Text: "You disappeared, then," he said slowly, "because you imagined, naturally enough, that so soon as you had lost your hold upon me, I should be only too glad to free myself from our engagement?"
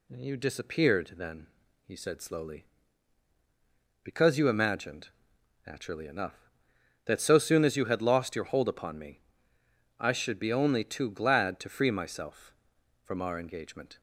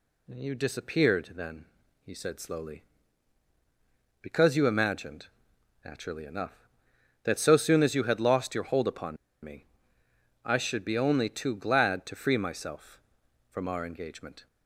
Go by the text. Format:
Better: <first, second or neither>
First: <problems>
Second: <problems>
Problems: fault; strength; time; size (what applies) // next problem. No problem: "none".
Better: first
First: none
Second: pauses between "upon" and "me"; slight; at 9.1 s; 0.28 s long